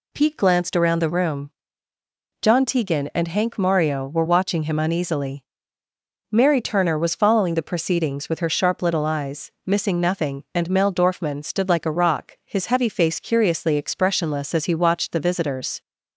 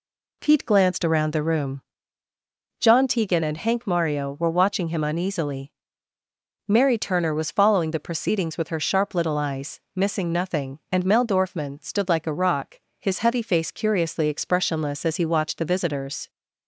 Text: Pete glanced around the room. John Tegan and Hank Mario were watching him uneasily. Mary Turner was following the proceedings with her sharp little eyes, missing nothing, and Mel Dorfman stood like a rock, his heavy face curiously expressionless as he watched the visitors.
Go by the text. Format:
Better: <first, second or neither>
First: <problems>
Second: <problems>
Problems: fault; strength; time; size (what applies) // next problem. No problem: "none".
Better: neither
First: none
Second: none